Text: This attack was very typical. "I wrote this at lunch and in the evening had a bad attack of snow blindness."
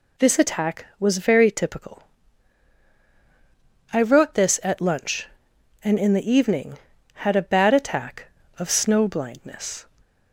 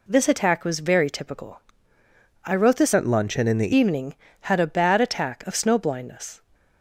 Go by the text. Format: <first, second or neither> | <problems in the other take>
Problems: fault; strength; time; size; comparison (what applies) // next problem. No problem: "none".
first | changes voice from "at" to "the"; from 2.9 to 3.7 s; 0.8 s long